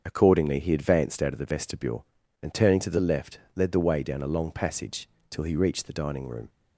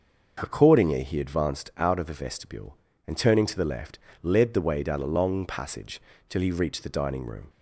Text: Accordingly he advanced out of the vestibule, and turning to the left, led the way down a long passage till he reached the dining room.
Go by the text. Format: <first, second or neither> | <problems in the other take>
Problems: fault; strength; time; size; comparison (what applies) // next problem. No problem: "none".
neither | starts louder than the rest; the same in both // pauses between "passage" and "till"; slight; the same in both